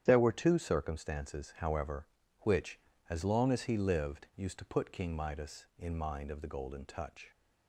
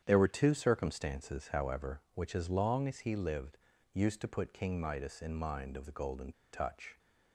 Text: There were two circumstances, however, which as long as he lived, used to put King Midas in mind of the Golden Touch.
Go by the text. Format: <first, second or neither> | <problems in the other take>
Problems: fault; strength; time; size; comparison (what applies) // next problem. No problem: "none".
first | starts louder than the rest; strong; until 1.0 s; 9 dB; strong in the first // pauses between "Golden" and "Touch"; slight; at 6.3 s; 0.20 s long